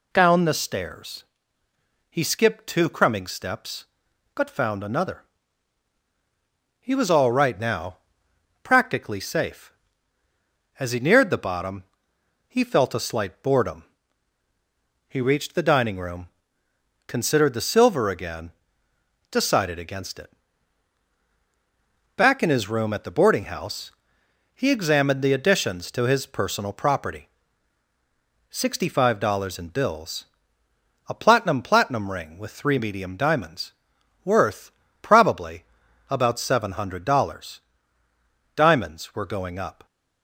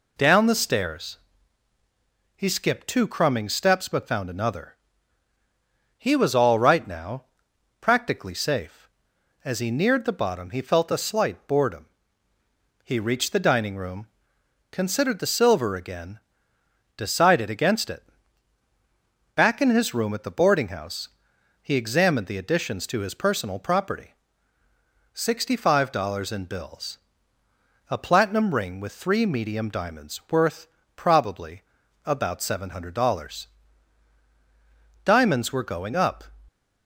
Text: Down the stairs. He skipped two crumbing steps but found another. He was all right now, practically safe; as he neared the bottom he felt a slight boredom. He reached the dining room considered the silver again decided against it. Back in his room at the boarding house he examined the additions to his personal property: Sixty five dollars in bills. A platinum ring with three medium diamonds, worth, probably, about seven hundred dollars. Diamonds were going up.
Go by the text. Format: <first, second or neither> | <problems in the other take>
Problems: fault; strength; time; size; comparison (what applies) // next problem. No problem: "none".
second | pauses between "bottom" and "he"; noticeable; at 11.8 s; 0.66 s long // pauses between "room" and "considered"; noticeable; at 16.2 s; 0.80 s long; noticeable in the second // pauses between "again" and "decided"; noticeable; at 18.5 s; 0.78 s long; noticeable in the second // pauses between "house" and "he"; noticeable; at 23.9 s; 0.64 s long; noticeable in the second // says "platinum" twice; at 31.6 s